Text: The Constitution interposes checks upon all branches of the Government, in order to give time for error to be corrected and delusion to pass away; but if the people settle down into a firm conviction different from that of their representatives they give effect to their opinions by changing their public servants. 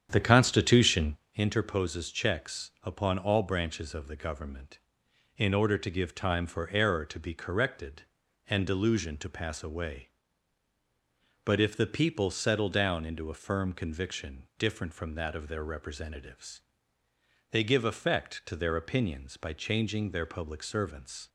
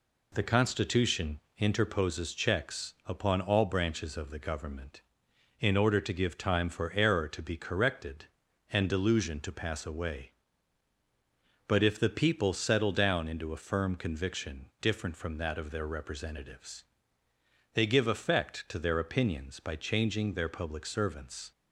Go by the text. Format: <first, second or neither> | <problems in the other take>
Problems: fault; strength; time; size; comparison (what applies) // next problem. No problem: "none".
second | starts louder than the rest; strong; until 1.2 s; 8.5 dB // pauses between "Constitution" and "interposes"; slight; at 1.1 s; 0.18 s long; slight in the second // pauses between "representatives" and "they"; noticeable; at 16.6 s; 0.92 s long; noticeable in the second